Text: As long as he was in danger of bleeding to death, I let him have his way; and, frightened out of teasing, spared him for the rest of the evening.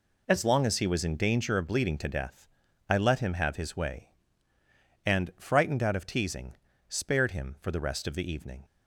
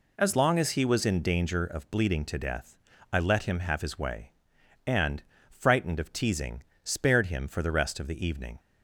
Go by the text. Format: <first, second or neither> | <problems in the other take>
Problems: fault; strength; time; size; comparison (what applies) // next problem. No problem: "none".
first | skips "out"; at 5.9 s